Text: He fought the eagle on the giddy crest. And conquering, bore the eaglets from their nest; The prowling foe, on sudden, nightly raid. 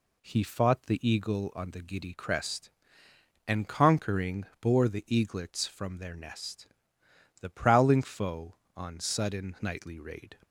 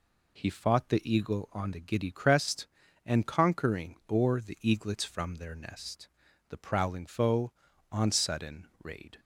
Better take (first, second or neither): first